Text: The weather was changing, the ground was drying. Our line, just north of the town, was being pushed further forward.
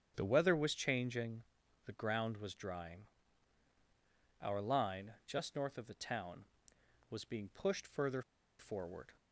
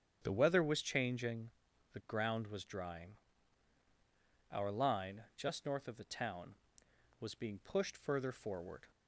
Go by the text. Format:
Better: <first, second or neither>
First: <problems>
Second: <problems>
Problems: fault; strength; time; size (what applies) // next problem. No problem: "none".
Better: second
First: starts louder than the rest; strong; until 1.1 s; 8.5 dB // pauses between "further" and "forward"; at 8.2 s; 0.37 s long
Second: starts louder than the rest; strong; until 1.2 s; 8.5 dB